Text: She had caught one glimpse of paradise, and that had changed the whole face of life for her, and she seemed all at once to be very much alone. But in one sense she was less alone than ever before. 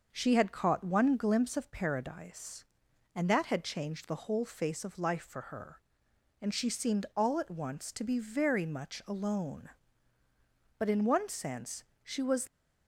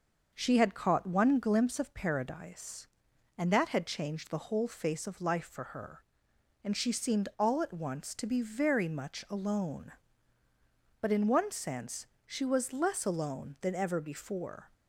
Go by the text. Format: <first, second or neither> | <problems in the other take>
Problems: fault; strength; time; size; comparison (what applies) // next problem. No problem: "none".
second | starts louder than the rest; noticeable; until 1.1 s; 6 dB; noticeable in the second // pauses between "sense" and "she"; slight; at 11.8 s; 0.18 s long; slight in the second // stops before "less alone than ever before"; at 12.4 s